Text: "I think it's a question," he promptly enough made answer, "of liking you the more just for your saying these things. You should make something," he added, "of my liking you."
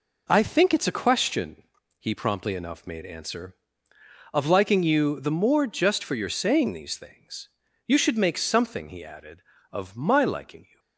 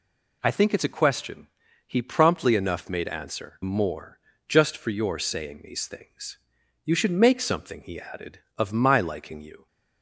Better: first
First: none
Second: skips "of liking you the"; at 3.6 s // pauses between "more" and "just"; slight; at 4.1 s; 0.30 s long

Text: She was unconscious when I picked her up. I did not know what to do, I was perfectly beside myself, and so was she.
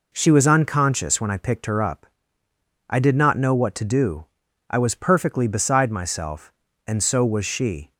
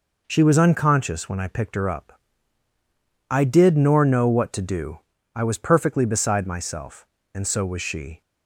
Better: first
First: none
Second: says "nor" for "not"; at 3.7 s

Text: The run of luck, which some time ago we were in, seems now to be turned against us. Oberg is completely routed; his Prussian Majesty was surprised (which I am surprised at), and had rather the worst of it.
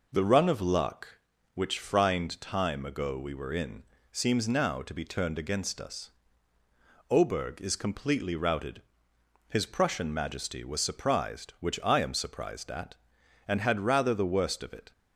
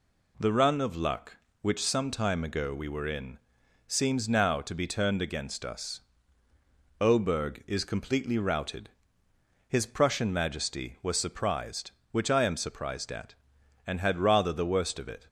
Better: second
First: says "frind" for "some"; at 1.7 s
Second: none

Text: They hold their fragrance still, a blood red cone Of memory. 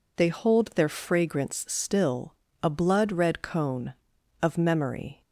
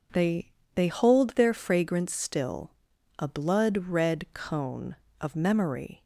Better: first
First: none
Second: says "They" twice; at 0.7 s

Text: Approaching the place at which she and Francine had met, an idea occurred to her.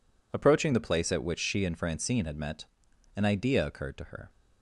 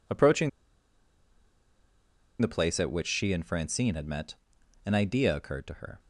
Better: first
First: none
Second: pauses between "Approaching" and "the"; strong; at 0.4 s; 1.9 s long

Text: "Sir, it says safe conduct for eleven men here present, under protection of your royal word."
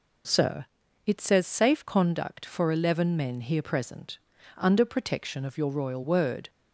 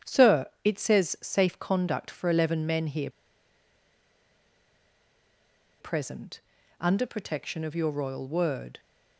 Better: first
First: none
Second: starts louder than the rest; strong; until 1.2 s; 9 dB // pauses between "here" and "present"; strong; at 3.0 s; 2.7 s long

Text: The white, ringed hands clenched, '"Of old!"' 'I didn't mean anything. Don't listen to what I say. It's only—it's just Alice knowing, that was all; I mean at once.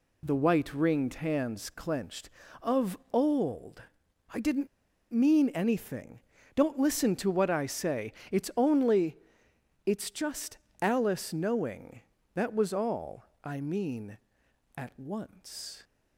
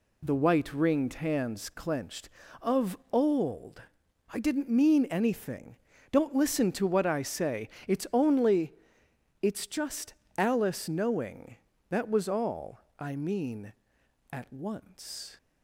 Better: second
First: pauses between "Of" and "old"; slight; at 2.9 s; 0.16 s long // pauses between "didn't" and "mean"; noticeable; at 4.6 s; 0.46 s long // pauses between "just" and "Alice"; slight; at 10.5 s; 0.24 s long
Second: pauses between "Of" and "old"; slight; at 2.9 s; 0.16 s long // pauses between "just" and "Alice"; slight; at 10.1 s; 0.24 s long

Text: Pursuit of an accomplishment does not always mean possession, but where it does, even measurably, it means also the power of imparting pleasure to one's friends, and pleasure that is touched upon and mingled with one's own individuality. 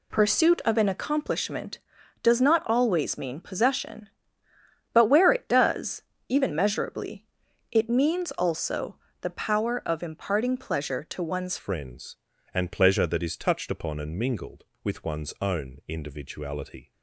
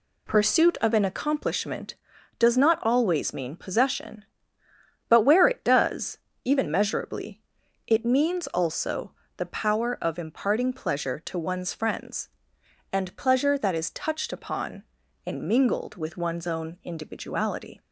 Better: second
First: pauses between "also" and "the"; slight; at 8.9 s; 0.24 s long // changes voice at "friends"; from 11.5 s on; 5.4 s long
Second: pauses between "also" and "the"; slight; at 9.1 s; 0.24 s long

